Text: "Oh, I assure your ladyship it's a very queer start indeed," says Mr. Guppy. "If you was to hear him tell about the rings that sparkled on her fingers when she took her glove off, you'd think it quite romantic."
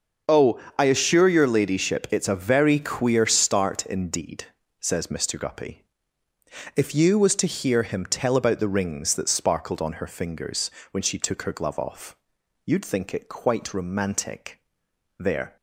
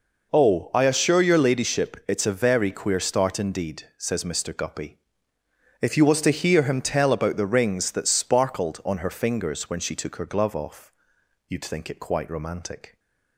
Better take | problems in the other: second | starts louder than the rest; until 1.4 s; 6 dB // pauses between "fingers" and "when"; slight; at 10.7 s; 0.22 s long // goes on to say "There"; slight; from 15.1 s on; 0.38 s long

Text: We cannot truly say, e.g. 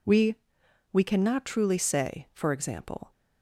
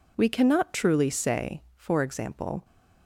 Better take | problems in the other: second | says "We" twice; at 0.9 s

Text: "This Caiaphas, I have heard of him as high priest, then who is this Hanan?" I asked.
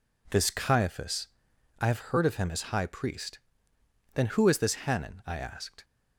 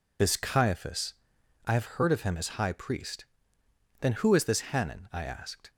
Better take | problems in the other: first | loses the start of "This"; at 0.1 s; 85 ms

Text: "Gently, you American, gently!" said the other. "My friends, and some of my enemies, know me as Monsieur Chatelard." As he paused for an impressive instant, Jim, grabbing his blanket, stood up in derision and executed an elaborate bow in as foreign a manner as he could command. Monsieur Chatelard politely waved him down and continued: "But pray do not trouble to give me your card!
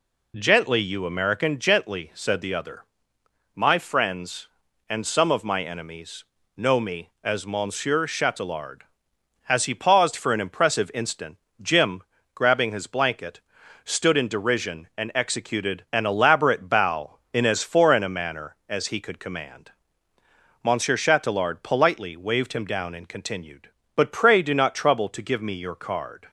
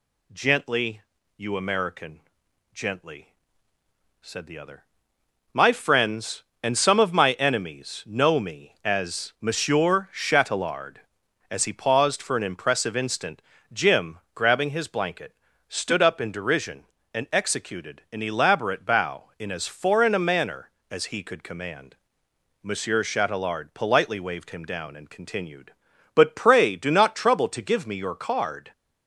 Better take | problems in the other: second | skips "up"; at 14.1 s

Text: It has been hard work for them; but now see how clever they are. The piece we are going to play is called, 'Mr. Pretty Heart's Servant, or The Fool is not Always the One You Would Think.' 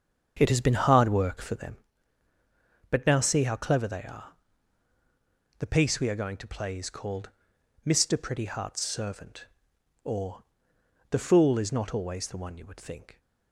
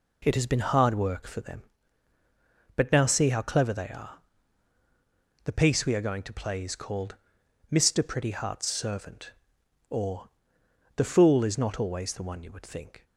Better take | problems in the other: second | starts louder than the rest; until 1.8 s; 7 dB // pauses between "or" and "The"; noticeable; at 10.4 s; 0.66 s long; noticeable in the second

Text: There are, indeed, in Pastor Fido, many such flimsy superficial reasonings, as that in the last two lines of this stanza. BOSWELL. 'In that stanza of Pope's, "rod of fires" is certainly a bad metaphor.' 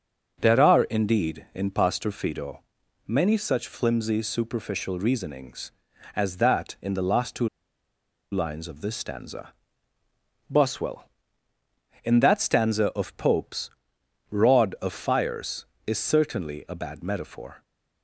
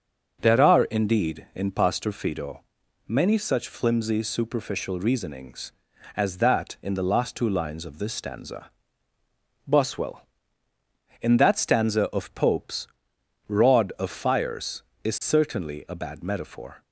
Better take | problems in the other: second | starts louder than the rest; until 1.4 s; 7 dB; also in the second // pauses between "two" and "lines"; noticeable; at 7.4 s; 0.83 s long

